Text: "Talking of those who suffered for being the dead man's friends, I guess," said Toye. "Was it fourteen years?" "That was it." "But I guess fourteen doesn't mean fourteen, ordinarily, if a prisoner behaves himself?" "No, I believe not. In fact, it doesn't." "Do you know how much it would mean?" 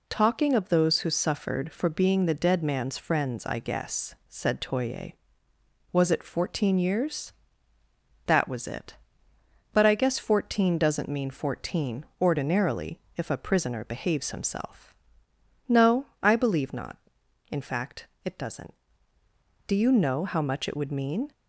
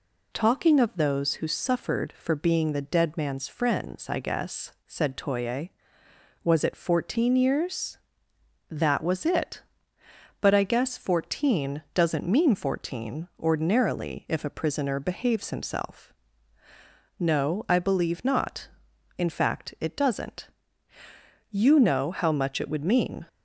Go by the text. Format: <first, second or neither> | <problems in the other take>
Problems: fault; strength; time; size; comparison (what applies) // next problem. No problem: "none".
first | skips "Do"; at 20.9 s